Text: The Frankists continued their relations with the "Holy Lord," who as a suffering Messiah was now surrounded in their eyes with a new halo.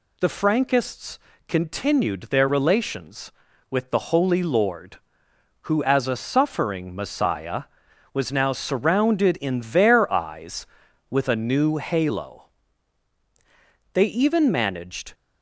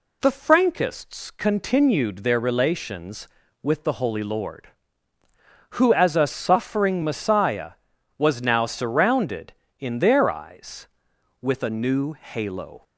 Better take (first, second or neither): second